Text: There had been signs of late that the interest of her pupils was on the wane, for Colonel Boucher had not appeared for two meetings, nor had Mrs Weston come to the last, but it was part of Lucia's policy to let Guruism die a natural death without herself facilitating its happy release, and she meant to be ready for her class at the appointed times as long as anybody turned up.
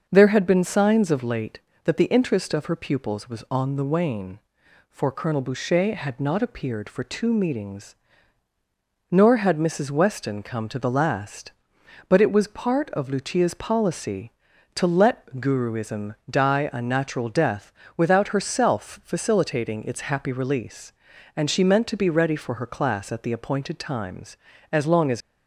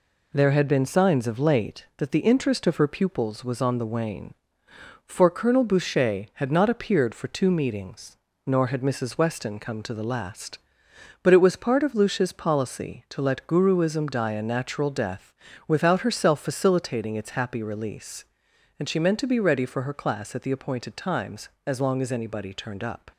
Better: second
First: pauses between "let" and "Guruism"; slight; at 15.2 s; 0.16 s long // pauses between "death" and "without"; slight; at 17.7 s; 0.24 s long // stops before "anybody turned up"; at 25.2 s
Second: pauses between "death" and "without"; slight; at 15.3 s; 0.32 s long

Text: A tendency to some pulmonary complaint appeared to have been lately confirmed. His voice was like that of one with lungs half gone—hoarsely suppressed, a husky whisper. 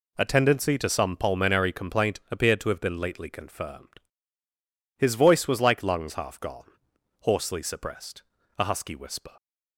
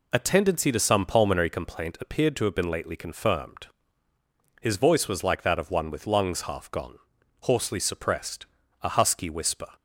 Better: second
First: skips "that of one with"; at 5.8 s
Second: none

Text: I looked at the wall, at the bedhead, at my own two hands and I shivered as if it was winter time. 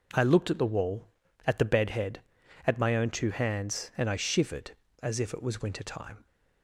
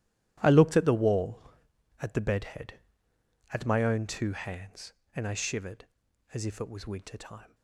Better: first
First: none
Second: gets quieter; strong; throughout; 15.5 dB

